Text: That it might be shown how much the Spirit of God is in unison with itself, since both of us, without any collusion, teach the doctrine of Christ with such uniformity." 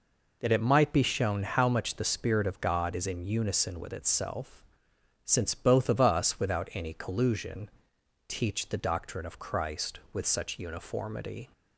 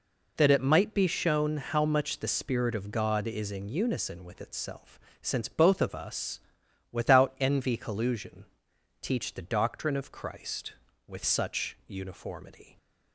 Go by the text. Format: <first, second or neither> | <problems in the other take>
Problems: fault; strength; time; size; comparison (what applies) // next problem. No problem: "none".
first | says "envy" for "any"; at 7.3 s